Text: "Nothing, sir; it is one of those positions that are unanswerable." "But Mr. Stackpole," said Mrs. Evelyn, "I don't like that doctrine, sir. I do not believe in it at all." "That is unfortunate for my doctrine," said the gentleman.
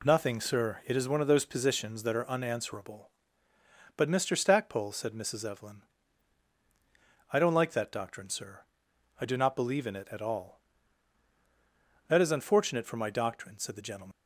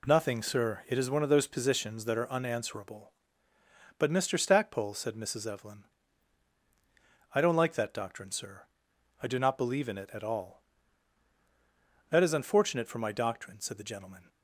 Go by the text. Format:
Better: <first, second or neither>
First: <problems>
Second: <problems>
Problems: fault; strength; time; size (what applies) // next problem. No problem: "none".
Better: second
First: leaves "gentleman" unfinished; at 14.1 s; 150 ms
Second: none